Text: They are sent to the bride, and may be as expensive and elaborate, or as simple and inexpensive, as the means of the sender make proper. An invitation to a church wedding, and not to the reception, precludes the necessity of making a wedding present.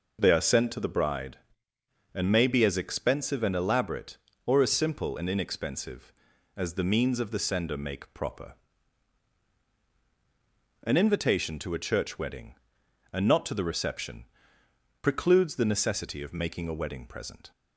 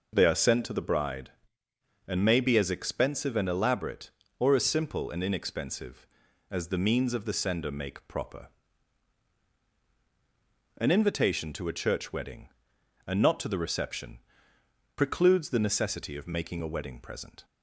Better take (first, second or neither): neither